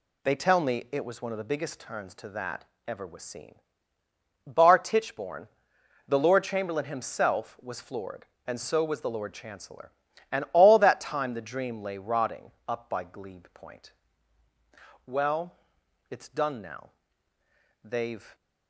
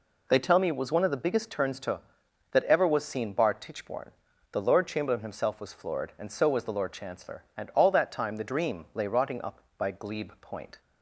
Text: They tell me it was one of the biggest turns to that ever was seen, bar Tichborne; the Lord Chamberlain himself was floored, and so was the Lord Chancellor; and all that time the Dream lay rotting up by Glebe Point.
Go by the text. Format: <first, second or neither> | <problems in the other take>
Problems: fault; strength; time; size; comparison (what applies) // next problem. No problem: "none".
second | pauses between "that" and "ever"; slight; at 2.6 s; 0.22 s long // pauses between "rotting" and "up"; slight; at 12.5 s; 0.16 s long // goes on to say "Well it's done now they've"; strong; from 15.0 s on; 3.2 s long